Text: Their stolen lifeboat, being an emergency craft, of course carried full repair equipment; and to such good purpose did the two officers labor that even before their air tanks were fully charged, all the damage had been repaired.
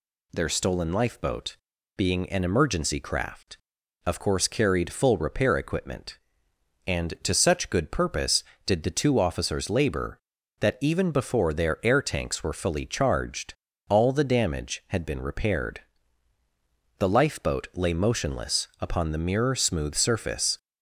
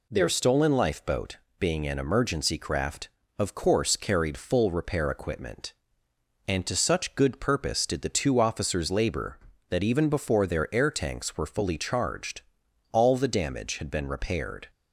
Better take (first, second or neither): second